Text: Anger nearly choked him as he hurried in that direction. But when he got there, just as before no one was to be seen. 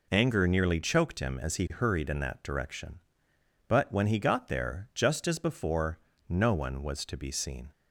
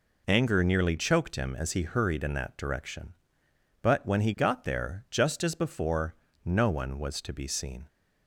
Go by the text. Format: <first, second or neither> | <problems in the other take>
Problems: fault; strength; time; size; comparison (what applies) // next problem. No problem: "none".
neither | pauses between "before" and "no"; slight; the same in both